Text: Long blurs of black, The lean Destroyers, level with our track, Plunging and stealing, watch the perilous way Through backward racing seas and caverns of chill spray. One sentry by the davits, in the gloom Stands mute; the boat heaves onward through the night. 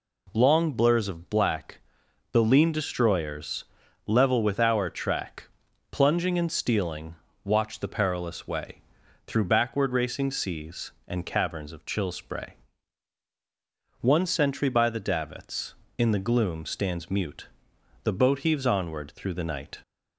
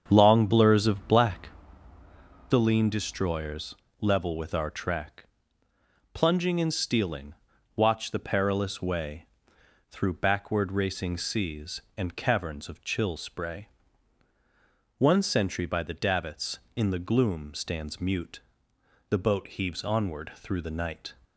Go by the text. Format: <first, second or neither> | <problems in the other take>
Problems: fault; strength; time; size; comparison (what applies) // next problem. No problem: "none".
first | starts louder than the rest; strong; until 1.7 s; 7.5 dB // pauses between "way" and "Through"; noticeable; at 9.2 s; 0.64 s long; also in the first